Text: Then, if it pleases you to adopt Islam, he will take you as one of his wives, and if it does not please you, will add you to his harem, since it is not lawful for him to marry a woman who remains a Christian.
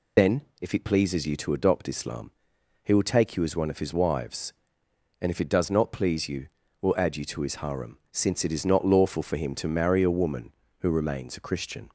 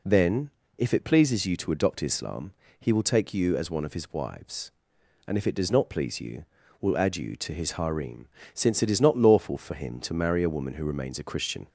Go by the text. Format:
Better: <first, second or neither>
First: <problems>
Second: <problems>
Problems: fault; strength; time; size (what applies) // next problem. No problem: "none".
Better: second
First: loses the start of "Then"; at 0.1 s; 70 ms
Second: none